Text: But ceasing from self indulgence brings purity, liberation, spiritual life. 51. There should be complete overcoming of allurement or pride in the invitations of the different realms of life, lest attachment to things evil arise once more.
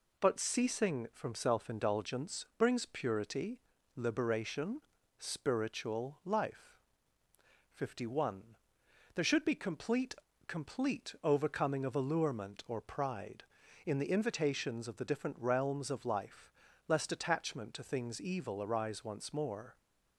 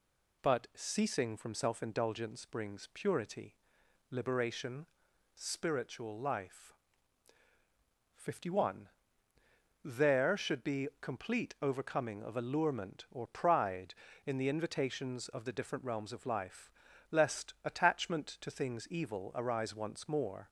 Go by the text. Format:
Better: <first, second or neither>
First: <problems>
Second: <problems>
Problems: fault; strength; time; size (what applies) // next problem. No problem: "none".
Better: second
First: says "complete" twice; at 10.4 s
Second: none